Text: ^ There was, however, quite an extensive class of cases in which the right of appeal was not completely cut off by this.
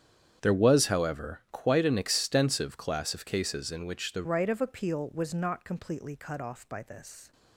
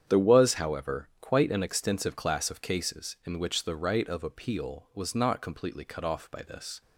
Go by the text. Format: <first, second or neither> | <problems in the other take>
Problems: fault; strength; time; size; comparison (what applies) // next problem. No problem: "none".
second | starts louder than the rest; strong; until 1.4 s; 8.5 dB; strong in the second // changes voice at "right"; from 4.2 s on; 3.1 s long